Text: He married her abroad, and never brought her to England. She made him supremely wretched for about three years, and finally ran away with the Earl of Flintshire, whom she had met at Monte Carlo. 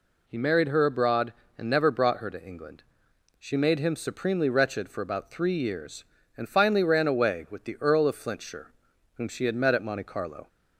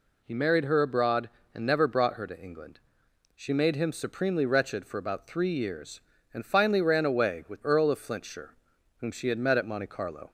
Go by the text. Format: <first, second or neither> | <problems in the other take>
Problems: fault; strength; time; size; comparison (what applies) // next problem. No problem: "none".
first | skips "the"; at 7.6 s